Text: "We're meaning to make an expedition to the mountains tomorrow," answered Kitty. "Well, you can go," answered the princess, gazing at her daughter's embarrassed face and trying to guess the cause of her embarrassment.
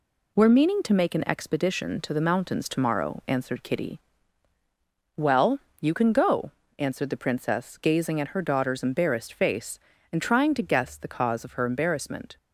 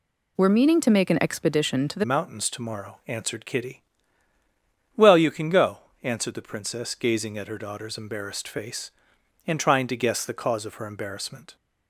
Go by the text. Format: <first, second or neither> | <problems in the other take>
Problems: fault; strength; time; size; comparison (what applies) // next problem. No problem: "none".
first | changes voice at "mountains"; from 2.0 s on; 9.5 s long